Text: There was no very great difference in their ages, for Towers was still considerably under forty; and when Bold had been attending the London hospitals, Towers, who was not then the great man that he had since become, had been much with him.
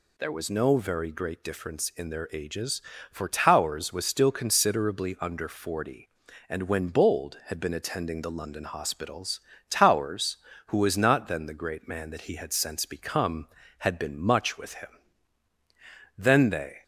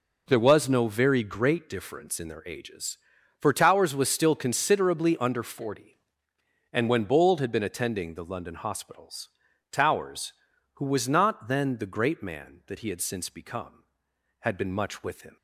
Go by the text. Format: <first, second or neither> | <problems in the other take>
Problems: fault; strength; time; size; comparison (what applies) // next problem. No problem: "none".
second | goes on to say "Then they"; noticeable; from 16.1 s on; 0.66 s long